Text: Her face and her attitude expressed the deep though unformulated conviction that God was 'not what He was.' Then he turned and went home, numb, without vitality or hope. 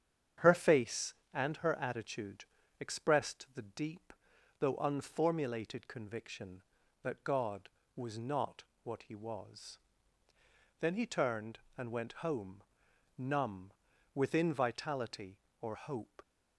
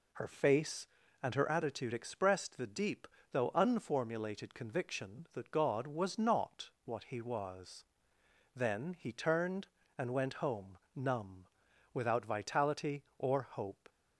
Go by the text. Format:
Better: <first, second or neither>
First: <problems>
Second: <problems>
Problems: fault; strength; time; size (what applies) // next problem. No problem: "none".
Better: second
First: starts louder than the rest; strong; until 1.5 s; 8.5 dB // pauses between "attitude" and "expressed"; slight; at 2.4 s; 0.34 s long // pauses between "deep" and "though"; noticeable; at 4.1 s; 0.48 s long // pauses between "not" and "what"; slight; at 8.6 s; 0.22 s long // says "within" for "without"; at 14.1 s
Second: pauses between "deep" and "though"; slight; at 3.0 s; 0.24 s long